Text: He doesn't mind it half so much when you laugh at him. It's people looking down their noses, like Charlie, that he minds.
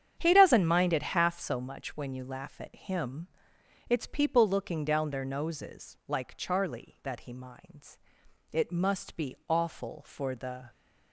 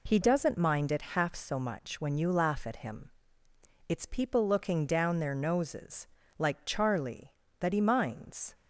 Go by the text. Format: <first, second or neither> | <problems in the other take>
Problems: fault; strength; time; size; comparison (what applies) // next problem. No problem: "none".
second | starts louder than the rest; strong; until 1.1 s; 8.5 dB // goes on to say "It must be awful for the"; strong; from 8.5 s on; 2.1 s long